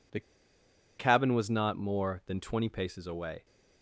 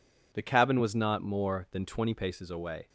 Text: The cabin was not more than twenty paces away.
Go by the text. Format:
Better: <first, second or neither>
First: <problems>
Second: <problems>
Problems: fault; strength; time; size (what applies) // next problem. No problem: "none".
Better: second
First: pauses between "The" and "cabin"; noticeable; at 0.1 s; 0.78 s long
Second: none